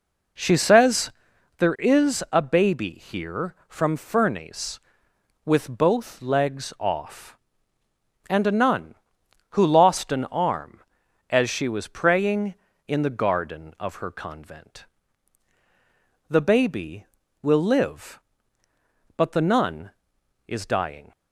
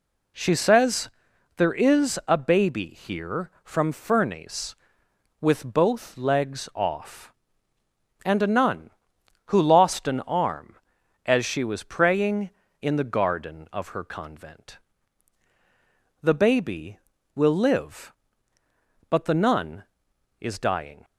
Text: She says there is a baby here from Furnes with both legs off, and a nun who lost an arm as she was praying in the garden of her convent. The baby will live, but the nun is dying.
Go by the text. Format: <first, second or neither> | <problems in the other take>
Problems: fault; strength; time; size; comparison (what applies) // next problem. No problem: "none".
second | starts louder than the rest; noticeable; until 1.6 s; 4.5 dB // pauses between "says" and "there"; noticeable; at 1.1 s; 0.46 s long; noticeable in the second